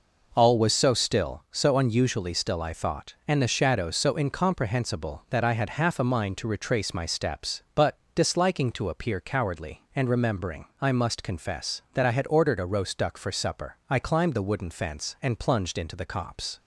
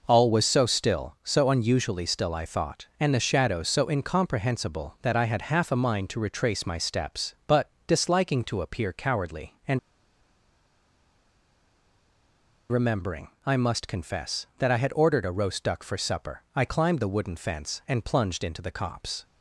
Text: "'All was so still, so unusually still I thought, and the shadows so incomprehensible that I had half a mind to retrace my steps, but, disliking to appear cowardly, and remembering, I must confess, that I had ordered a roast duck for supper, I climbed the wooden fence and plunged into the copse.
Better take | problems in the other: first | pauses between "and" and "remembering"; strong; at 9.7 s; 2.9 s long

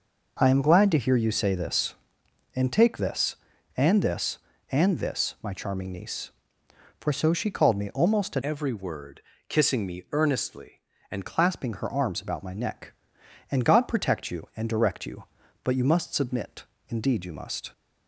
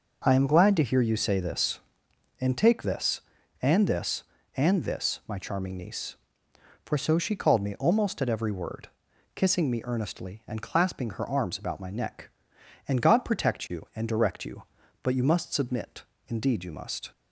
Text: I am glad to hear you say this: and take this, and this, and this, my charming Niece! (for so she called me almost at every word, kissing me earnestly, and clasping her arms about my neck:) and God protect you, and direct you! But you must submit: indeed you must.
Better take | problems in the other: second | changes voice from "every" to "and"; from 8.4 to 11.2 s; 2.8 s long

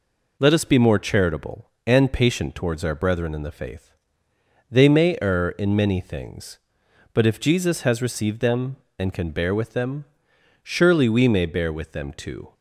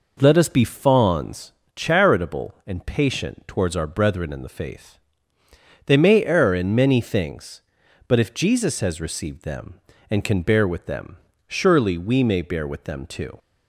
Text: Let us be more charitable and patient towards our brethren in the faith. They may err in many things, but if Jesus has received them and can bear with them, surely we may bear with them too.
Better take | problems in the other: first | says "fawns" for "more"; at 0.6 s

